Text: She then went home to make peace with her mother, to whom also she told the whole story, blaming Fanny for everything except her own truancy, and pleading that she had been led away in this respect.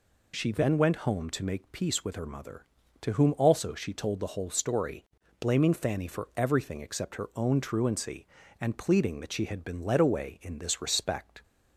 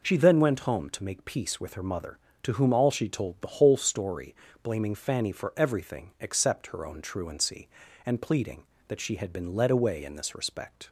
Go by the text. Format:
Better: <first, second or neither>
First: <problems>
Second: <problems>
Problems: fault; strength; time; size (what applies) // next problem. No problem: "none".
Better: first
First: none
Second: says "all" for "also"; at 2.7 s